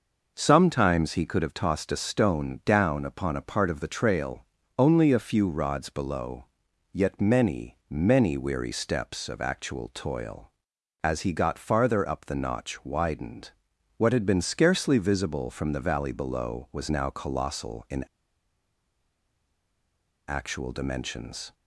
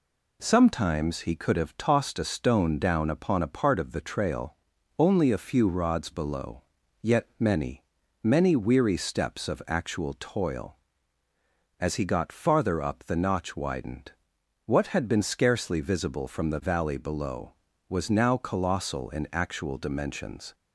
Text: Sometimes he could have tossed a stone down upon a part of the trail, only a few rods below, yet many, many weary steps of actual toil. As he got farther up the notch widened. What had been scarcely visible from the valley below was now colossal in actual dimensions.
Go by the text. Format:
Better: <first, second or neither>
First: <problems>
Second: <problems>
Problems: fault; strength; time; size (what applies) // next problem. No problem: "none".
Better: second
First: pauses between "in" and "actual"; strong; at 18.0 s; 2.2 s long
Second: none